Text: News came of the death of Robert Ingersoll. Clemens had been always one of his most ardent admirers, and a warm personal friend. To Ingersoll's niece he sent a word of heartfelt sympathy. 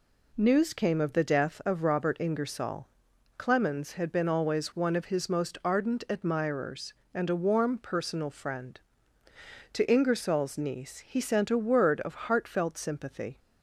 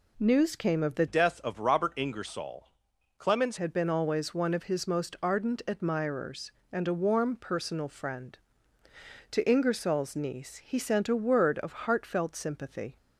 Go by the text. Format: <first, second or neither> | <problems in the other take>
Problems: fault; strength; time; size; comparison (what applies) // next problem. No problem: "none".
first | changes voice from "death" to "Clemens"; from 1.0 to 3.5 s; 2.5 s long